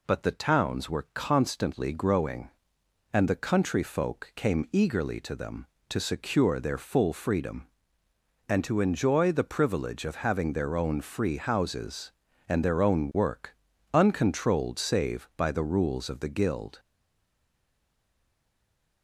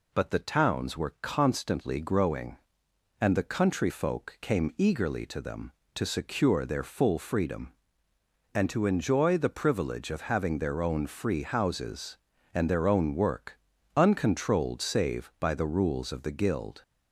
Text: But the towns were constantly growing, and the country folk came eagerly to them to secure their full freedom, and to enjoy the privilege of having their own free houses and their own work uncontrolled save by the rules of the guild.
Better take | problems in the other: second | pauses between "work" and "uncontrolled"; at 13.5 s; 0.40 s long; also in the second // stays silent after the last word; from 16.7 s on; 2.3 s long

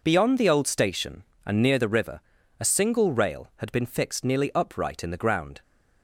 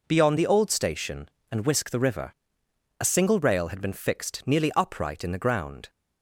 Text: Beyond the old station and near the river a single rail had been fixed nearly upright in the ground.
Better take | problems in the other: first | says "whisk" for "near"; at 1.6 s // pauses between "river" and "a"; noticeable; at 2.3 s; 0.66 s long; also in the first

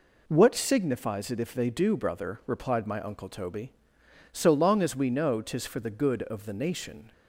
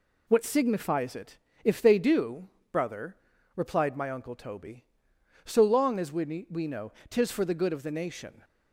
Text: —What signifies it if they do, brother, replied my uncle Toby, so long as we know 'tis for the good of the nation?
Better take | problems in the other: first | pauses between "it" and "if"; slight; at 1.3 s; 0.26 s long // says "we" twice; at 6.5 s // pauses between "know" and "tis"; slight; at 6.9 s; 0.16 s long

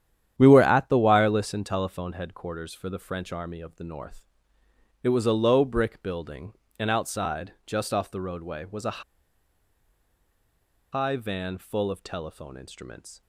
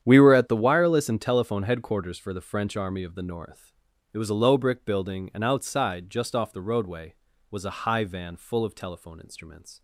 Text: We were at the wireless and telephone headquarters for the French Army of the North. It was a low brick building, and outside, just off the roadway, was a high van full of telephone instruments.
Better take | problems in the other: second | starts louder than the rest; strong; until 1.3 s; 10 dB; strong in the second // pauses between "a" and "high"; strong; at 9.0 s; 1.9 s long

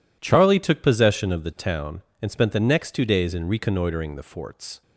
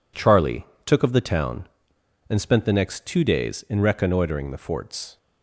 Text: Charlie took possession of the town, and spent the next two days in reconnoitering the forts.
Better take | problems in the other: first | pauses between "Charlie" and "took"; slight; at 0.6 s; 0.20 s long // skips "possession"; at 1.0 s

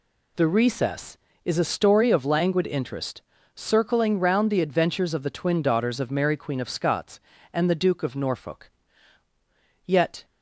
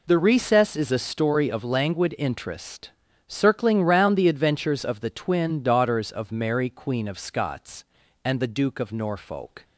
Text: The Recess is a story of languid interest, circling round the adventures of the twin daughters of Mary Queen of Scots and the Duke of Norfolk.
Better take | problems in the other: second | goes on to say "Yet"; slight; from 9.8 s on; 0.40 s long

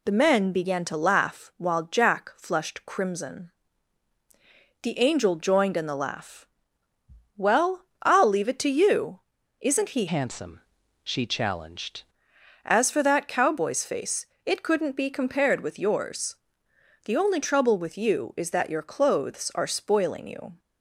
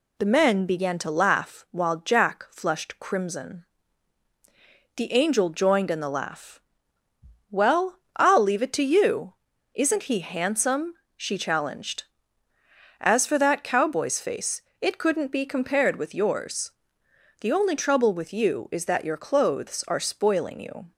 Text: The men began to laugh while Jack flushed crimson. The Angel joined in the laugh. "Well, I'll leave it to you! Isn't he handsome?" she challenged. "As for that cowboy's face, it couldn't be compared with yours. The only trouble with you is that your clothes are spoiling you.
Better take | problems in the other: second | changes voice from "handsome" to "challenged"; from 10.0 to 12.0 s; 2.0 s long

